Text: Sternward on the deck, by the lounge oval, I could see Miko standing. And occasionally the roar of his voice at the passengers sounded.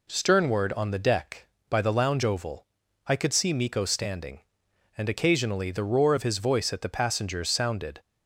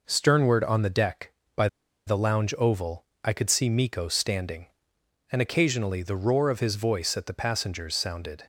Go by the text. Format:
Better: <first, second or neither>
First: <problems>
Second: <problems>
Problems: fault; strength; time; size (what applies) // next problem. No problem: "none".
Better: first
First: none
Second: pauses between "by" and "the"; at 1.6 s; 0.40 s long